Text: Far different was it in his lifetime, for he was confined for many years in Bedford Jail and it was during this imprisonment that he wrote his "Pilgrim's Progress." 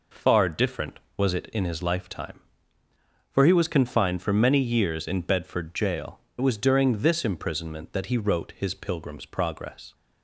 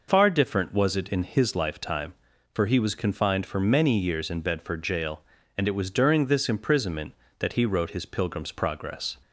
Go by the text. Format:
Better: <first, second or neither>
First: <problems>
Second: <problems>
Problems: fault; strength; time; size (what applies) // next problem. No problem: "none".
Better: second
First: skips "and"; at 6.2 s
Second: none